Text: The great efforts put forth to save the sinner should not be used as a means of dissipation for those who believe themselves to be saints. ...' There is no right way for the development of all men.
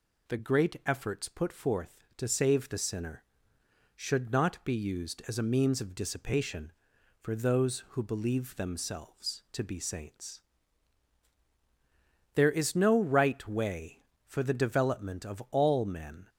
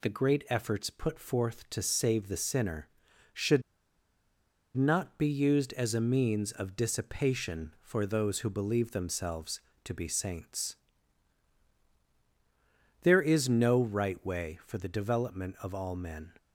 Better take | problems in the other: first | pauses between "should" and "not"; at 3.6 s; 1.1 s long

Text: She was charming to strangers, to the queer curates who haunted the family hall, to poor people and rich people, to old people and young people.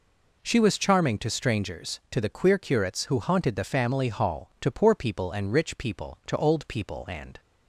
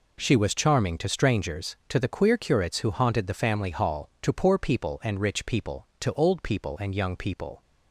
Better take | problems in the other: second | stops before "young people"; at 7.3 s

